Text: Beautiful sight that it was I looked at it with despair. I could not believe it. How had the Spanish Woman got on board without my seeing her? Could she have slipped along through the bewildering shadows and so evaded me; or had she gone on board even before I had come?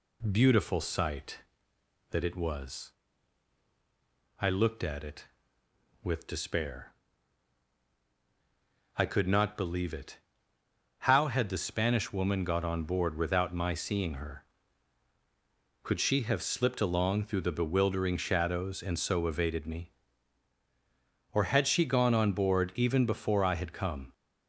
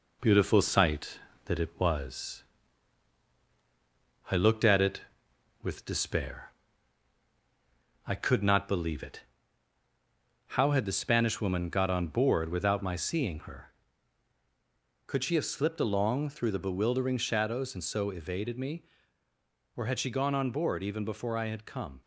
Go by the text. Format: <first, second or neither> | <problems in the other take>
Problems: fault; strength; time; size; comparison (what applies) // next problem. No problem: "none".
first | gets quieter; slight; throughout; 2.5 dB // pauses between "was" and "I"; strong; at 2.4 s; 1.8 s long; strong in the first